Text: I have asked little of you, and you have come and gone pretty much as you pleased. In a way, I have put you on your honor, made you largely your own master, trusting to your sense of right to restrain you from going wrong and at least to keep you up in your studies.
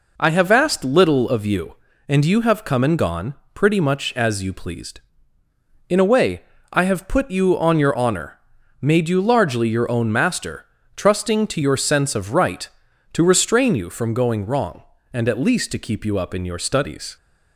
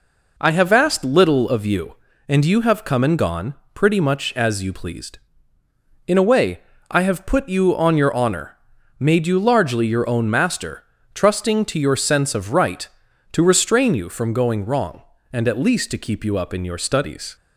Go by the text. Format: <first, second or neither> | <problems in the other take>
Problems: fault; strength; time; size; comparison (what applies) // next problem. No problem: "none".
neither | pauses between "gone" and "pretty"; slight; the same in both